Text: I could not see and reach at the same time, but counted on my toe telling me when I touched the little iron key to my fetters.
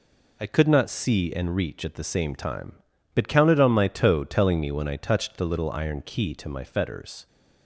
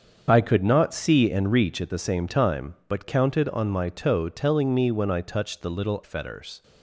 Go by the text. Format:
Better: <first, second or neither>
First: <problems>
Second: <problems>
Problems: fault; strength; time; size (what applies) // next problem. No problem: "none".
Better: first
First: none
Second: starts louder than the rest; strong; until 1.2 s; 7 dB // skips "iron key to my"; at 6.0 s